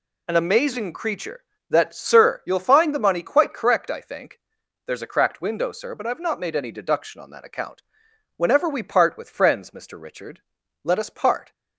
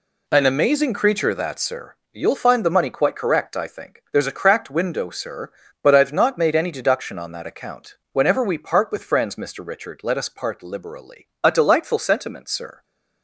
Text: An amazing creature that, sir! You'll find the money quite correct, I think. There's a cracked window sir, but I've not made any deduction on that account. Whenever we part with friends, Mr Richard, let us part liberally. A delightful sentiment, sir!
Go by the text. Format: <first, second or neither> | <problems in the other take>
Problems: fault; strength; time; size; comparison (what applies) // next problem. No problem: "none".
second | stops before "liberally A delightful sentiment sir"; at 11.5 s